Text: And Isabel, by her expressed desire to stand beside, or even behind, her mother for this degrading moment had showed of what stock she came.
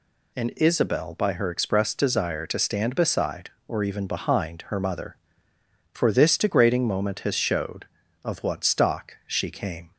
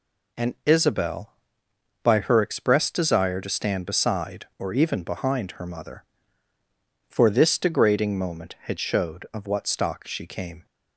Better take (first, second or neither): second